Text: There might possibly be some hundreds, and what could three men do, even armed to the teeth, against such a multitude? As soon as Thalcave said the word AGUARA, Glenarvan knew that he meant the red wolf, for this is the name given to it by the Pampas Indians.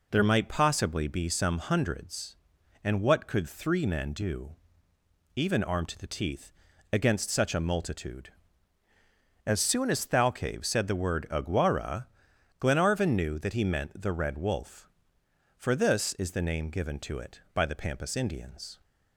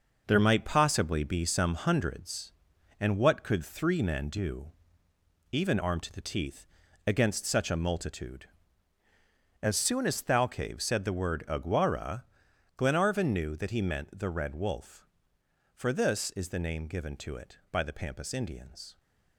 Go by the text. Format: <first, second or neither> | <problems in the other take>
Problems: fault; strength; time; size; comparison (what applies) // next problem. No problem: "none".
first | gets quieter; strong; throughout; 7.5 dB